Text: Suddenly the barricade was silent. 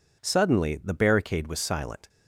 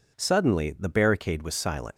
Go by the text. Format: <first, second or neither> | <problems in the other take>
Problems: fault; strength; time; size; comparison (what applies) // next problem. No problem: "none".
first | leaves "silent" unfinished; at 1.9 s; 70 ms